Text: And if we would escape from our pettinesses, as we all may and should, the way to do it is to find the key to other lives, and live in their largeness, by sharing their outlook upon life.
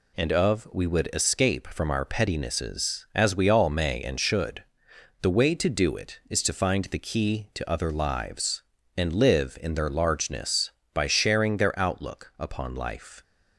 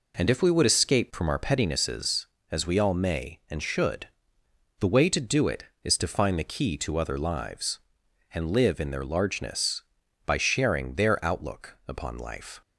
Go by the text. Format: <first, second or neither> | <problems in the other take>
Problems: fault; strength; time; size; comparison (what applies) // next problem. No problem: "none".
second | says "of" for "if"; at 0.3 s